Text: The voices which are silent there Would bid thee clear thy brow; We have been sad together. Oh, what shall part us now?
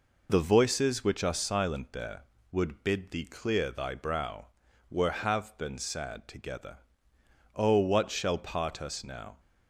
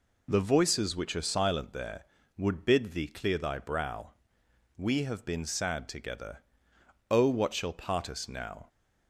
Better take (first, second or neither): second